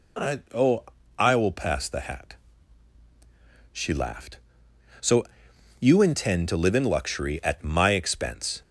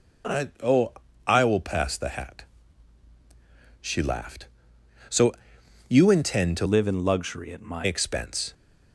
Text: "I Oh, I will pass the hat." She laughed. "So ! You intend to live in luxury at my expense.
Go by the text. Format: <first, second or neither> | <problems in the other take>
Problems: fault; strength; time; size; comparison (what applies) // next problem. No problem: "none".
first | changes voice from "live" to "my"; from 6.6 to 7.8 s; 1.2 s long